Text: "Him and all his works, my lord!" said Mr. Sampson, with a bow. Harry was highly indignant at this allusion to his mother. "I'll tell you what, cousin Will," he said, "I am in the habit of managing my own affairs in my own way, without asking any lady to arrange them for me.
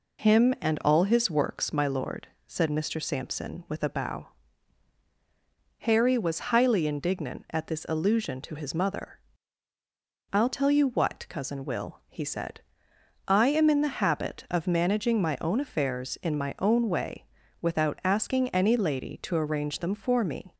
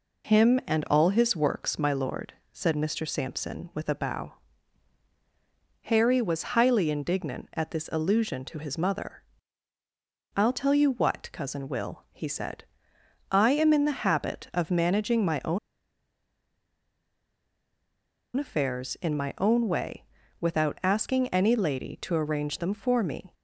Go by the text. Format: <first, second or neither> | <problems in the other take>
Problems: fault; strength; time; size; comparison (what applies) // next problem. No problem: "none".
first | pauses between "own" and "affairs"; strong; at 15.5 s; 2.7 s long